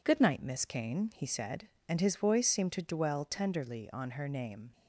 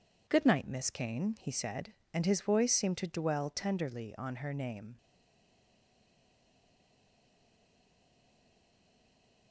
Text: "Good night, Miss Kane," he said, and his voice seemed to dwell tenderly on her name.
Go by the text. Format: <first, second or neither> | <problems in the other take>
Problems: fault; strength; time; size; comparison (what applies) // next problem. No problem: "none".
first | stays silent after the last word; strong; from 4.9 s on; 4.6 s long